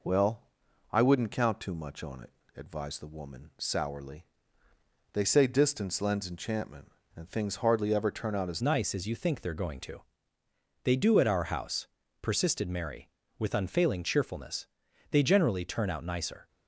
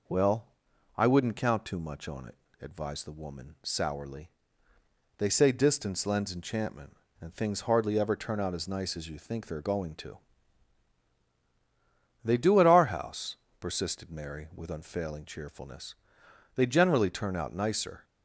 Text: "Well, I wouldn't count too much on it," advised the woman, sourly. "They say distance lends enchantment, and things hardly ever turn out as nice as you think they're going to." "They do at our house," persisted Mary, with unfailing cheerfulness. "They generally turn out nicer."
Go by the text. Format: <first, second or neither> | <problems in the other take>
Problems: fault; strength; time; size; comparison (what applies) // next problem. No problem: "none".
second | changes voice at "nice"; from 8.6 s on; 7.8 s long